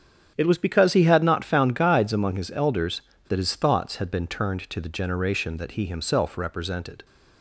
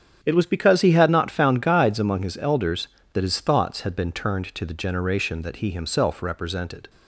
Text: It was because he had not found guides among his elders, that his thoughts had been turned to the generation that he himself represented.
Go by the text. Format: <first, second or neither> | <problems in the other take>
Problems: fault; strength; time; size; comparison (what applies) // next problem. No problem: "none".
neither | starts louder than the rest; strong; the same in both